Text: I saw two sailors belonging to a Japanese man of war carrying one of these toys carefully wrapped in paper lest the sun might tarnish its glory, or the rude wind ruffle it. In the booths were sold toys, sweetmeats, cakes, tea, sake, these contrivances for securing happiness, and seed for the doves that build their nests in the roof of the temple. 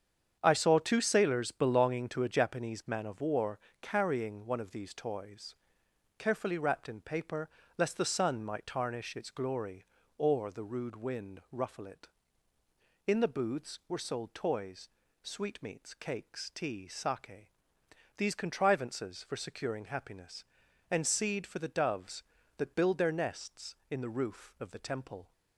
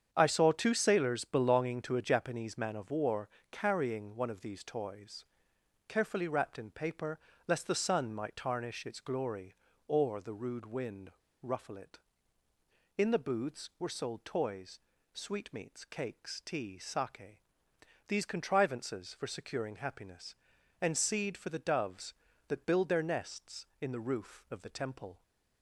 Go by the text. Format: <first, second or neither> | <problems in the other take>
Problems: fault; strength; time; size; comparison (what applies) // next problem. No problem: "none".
first | starts louder than the rest; strong; until 1.1 s; 8 dB; strong in the first // pauses between "war" and "carrying"; slight; at 3.2 s; 0.20 s long; slight in the first // pauses between "toys" and "carefully"; noticeable; at 5.2 s; 0.64 s long; noticeable in the first // pauses between "paper" and "lest"; slight; at 7.1 s; 0.30 s long; slight in the first // pauses between "wind" and "ruffle"; slight; at 11.1 s; 0.30 s long